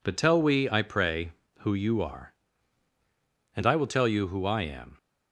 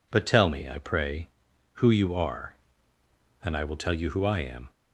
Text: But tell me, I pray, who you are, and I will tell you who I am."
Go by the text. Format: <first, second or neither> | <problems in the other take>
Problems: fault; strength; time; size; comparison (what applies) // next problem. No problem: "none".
second | says "we" for "me"; at 0.4 s